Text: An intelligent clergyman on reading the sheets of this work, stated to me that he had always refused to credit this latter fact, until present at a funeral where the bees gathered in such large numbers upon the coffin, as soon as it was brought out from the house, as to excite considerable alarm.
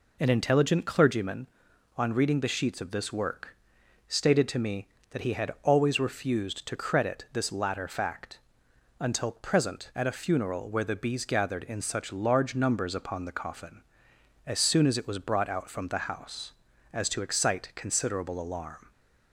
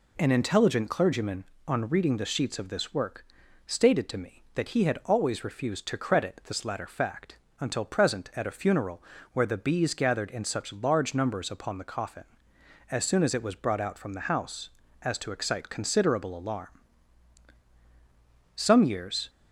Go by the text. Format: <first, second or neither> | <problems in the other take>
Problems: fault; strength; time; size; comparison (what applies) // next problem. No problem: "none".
first | pauses between "funeral" and "where"; slight; at 9.0 s; 0.32 s long // goes on to say "Some years"; noticeable; from 18.5 s on; 0.74 s long